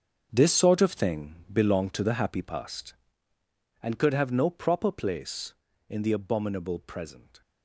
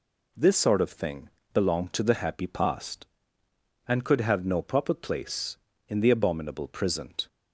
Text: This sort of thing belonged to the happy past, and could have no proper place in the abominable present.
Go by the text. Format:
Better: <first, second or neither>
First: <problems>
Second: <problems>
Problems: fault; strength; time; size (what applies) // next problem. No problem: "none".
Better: second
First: gets quieter; strong; throughout; 14 dB // pauses between "thing" and "belonged"; slight; at 1.3 s; 0.18 s long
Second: pauses between "thing" and "belonged"; slight; at 1.2 s; 0.24 s long